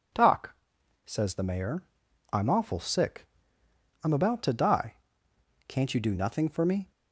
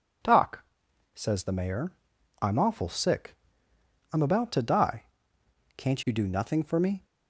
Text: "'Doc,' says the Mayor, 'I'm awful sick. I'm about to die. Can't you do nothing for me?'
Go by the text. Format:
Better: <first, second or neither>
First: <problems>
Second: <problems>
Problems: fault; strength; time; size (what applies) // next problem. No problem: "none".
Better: neither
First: none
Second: none